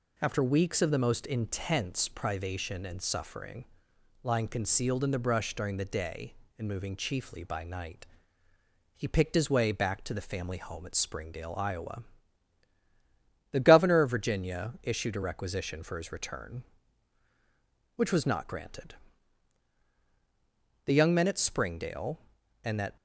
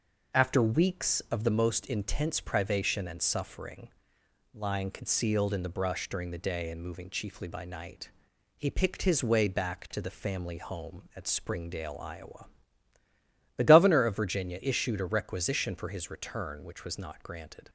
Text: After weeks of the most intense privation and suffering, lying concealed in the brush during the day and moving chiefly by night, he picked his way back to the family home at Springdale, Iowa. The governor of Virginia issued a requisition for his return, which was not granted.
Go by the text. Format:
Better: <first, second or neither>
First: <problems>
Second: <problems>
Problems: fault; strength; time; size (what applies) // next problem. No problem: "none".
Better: second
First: goes on to say "The young men at Springdale and that"; strong; from 20.8 s on; 2.1 s long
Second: none